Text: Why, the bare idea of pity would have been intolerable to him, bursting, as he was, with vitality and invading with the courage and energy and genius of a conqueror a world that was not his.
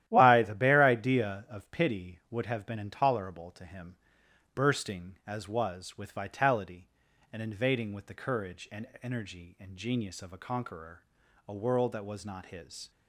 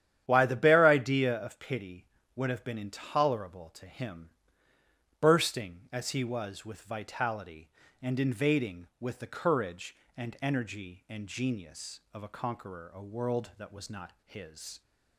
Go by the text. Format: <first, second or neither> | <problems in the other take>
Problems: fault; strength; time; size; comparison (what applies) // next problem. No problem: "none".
second | starts louder than the rest; strong; until 1.1 s; 12.5 dB; strong in the second // skips "he"; at 5.4 s // pauses between "and" and "energy"; slight; at 8.8 s; 0.16 s long // pauses between "conqueror" and "a"; at 11.0 s; 0.42 s long